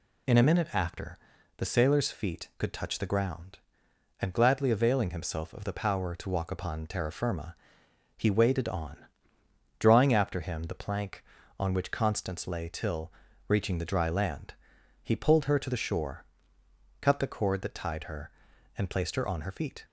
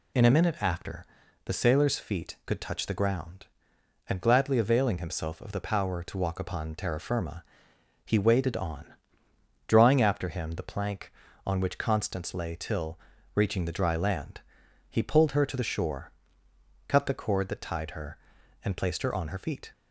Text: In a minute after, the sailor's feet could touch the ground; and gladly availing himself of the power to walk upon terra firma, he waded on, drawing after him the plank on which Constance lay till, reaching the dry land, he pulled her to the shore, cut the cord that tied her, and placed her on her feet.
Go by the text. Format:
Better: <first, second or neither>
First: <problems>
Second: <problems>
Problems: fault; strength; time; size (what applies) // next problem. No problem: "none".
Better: neither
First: none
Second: none